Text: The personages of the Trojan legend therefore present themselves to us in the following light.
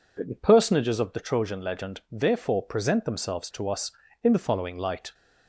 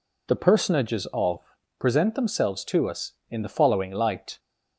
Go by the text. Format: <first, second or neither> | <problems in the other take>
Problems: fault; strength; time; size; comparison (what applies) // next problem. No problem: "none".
first | skips "the Trojan legend therefore"; at 1.6 s